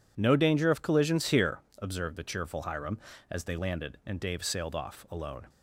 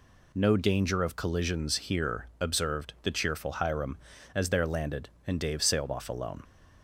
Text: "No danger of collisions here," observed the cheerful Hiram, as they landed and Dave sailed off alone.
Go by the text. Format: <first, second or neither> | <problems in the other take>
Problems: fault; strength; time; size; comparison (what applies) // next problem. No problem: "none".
first | says "there" for "they"; at 4.5 s